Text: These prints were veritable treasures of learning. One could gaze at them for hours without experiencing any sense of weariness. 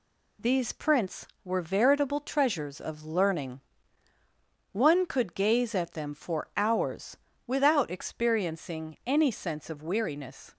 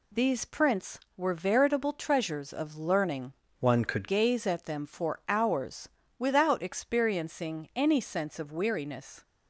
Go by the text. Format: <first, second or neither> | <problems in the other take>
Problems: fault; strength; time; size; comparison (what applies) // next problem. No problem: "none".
first | changes voice from "One" to "could"; from 3.6 to 4.0 s; 0.4 s long // pauses between "hours" and "without"; slight; at 5.8 s; 0.28 s long; slight in the first